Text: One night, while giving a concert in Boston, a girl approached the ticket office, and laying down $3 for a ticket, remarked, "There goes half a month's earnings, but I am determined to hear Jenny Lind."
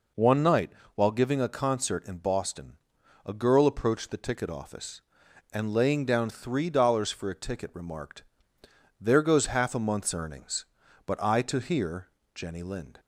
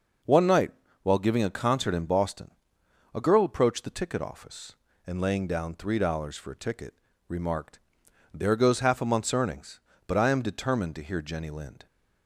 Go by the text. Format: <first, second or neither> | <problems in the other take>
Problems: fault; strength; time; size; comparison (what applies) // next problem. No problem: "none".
second | skips "am determined"; at 11.4 s // pauses between "hear" and "Jenny"; slight; at 12.0 s; 0.26 s long